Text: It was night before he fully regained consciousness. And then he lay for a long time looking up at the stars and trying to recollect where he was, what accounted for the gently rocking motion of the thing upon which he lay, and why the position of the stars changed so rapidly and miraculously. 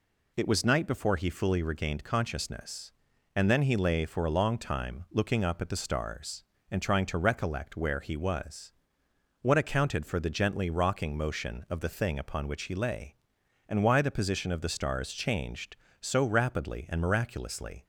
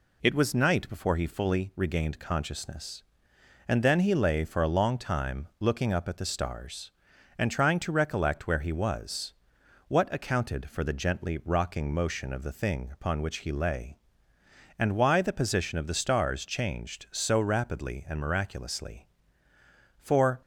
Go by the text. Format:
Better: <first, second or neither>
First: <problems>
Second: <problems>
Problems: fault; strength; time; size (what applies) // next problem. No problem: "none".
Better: first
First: none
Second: goes on to say "For"; slight; from 19.9 s on; 0.42 s long